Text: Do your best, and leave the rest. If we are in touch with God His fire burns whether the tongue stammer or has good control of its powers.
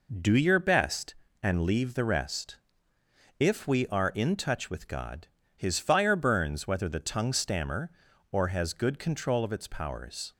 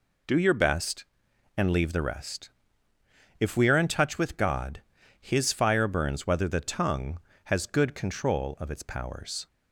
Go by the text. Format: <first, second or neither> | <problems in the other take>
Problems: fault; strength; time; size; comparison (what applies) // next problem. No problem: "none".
first | pauses between "God" and "His"; at 4.8 s; 0.40 s long; slight in the first // skips "stammer or"; at 7.3 s